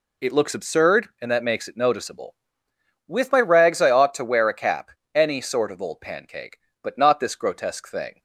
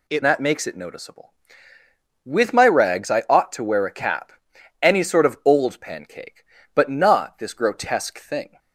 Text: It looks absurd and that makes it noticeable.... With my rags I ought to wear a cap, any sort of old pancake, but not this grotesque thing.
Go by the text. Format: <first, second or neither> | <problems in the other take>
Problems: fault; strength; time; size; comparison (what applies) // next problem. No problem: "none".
first | skips "looks absurd and"; at 0.2 s